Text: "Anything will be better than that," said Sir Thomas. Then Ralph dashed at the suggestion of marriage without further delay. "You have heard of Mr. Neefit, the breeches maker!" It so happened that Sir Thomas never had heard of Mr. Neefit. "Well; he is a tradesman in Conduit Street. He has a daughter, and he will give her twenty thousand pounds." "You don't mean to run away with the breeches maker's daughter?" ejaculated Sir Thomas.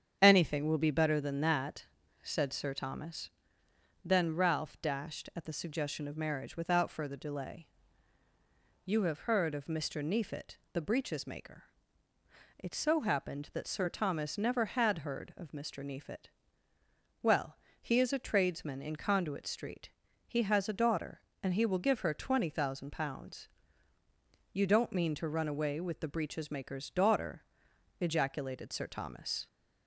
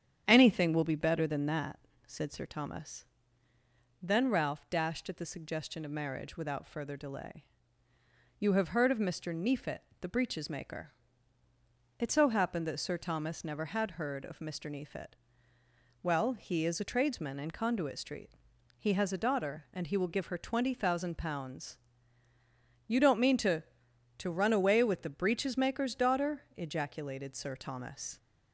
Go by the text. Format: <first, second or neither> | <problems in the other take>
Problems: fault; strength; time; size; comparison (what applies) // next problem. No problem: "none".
first | starts louder than the rest; strong; until 1.2 s; 9 dB; strong in the first // says "to" twice; at 24.1 s